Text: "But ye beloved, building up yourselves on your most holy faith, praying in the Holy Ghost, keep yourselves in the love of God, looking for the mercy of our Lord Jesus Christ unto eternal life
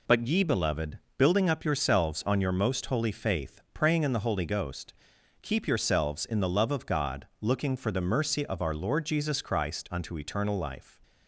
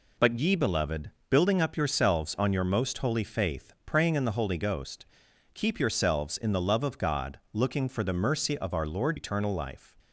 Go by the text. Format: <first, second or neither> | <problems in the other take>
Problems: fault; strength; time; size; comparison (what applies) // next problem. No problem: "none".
first | skips "Jesus Christ unto"; at 9.1 s